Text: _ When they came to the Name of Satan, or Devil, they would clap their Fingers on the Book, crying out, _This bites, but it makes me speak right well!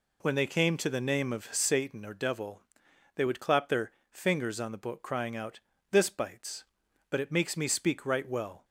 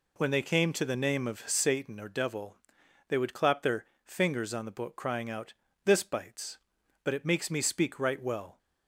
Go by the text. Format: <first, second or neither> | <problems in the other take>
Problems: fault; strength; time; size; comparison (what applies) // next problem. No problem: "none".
neither | pauses between "their" and "Fingers"; slight; the same in both